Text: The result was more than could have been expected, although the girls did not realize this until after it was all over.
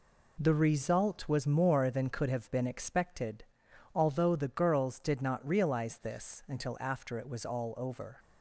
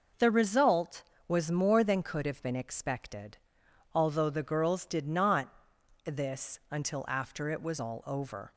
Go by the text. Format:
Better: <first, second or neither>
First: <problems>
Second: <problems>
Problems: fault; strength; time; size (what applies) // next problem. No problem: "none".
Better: first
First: none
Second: skips "realize"; at 5.7 s